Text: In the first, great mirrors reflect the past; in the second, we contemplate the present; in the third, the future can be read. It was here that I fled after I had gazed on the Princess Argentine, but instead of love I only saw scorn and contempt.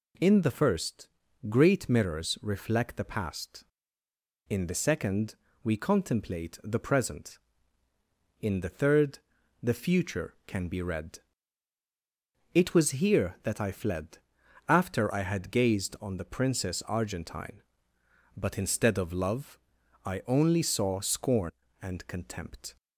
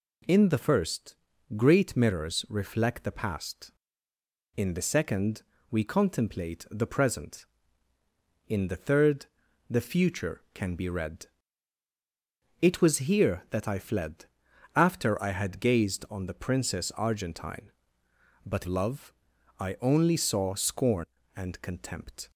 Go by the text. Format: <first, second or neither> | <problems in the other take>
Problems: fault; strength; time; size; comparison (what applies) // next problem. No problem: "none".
first | pauses between "fled" and "after"; noticeable; at 14.2 s; 0.54 s long; noticeable in the first // skips "instead of"; at 18.6 s // pauses between "love" and "I"; noticeable; at 19.1 s; 0.48 s long; noticeable in the first